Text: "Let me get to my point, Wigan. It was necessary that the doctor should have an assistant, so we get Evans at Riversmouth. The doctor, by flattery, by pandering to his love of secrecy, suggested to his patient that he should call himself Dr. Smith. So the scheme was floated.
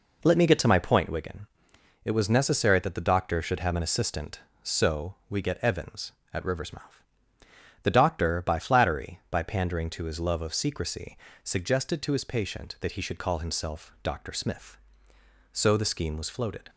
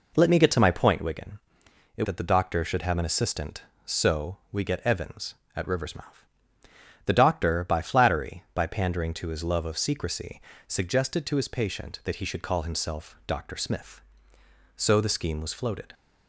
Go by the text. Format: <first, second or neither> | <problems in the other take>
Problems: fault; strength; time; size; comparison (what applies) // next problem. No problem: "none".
first | skips "was necessary"; at 2.0 s